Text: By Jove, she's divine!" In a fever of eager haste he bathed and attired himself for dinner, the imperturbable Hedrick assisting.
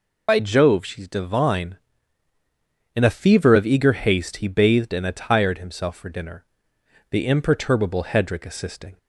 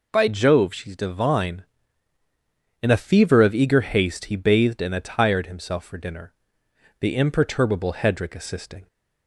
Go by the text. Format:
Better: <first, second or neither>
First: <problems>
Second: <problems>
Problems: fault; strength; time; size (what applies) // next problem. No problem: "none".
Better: second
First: loses the start of "By"; at 0.2 s; 65 ms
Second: none